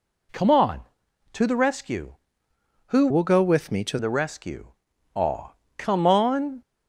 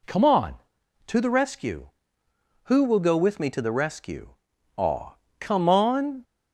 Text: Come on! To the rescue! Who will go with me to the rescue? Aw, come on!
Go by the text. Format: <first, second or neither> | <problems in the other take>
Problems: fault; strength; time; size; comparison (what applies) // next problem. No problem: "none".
second | changes voice from "will" to "to"; from 3.1 to 3.9 s; 0.8 s long